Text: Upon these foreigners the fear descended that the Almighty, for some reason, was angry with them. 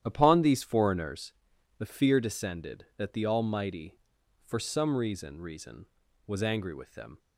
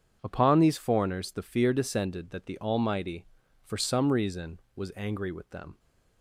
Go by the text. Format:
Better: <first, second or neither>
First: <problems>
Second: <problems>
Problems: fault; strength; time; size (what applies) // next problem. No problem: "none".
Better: second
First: starts louder than the rest; strong; until 1.0 s; 11 dB // pauses between "foreigners" and "the"; noticeable; at 1.3 s; 0.46 s long // says "reason" twice; at 5.4 s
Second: starts louder than the rest; strong; until 1.2 s; 8 dB